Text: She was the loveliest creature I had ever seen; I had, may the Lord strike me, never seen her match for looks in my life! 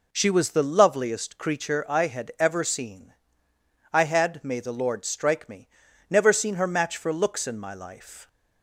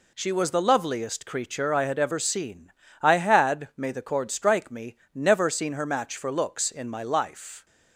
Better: first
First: none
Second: says "Cord" for "Lord"; at 4.0 s

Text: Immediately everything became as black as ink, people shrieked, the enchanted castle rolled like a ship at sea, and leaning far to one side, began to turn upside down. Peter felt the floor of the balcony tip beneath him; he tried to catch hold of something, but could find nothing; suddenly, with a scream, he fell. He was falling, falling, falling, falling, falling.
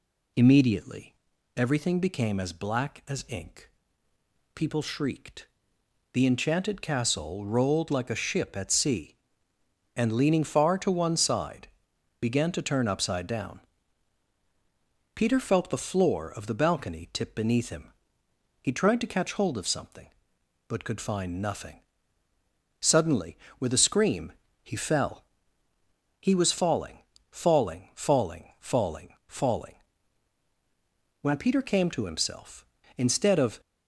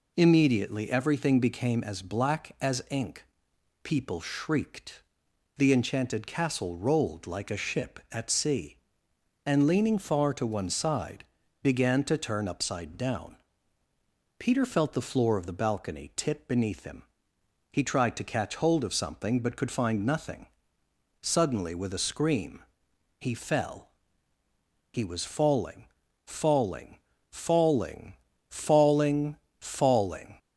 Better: second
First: pauses between "Immediately" and "everything"; at 1.1 s; 0.42 s long // goes on to say "When Peter came to himself instead of"; strong; from 31.1 s on; 2.4 s long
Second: none

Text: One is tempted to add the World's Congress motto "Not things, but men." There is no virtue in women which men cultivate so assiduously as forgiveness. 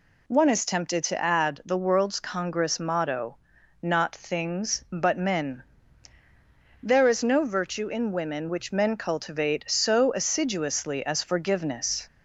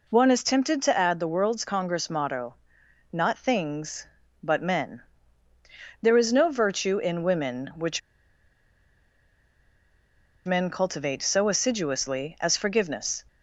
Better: first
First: pauses between "motto" and "Not"; at 3.3 s; 0.44 s long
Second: pauses between "motto" and "Not"; noticeable; at 2.5 s; 0.56 s long // pauses between "which" and "men"; strong; at 8.0 s; 2.4 s long

